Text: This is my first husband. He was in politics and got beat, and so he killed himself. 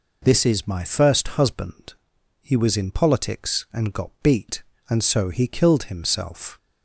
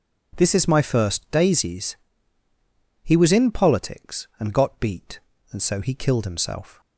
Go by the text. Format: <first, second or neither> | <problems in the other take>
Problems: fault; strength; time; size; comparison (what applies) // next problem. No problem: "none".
first | says "daisies" for "husband"; at 1.3 s